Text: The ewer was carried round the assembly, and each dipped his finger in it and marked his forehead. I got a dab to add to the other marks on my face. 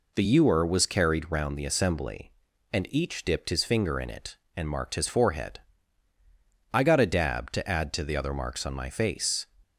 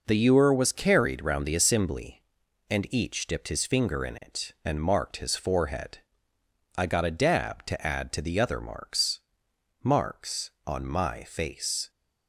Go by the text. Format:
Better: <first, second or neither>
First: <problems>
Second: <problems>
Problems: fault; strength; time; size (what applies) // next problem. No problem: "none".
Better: first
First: none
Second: says "marks" twice; at 9.8 s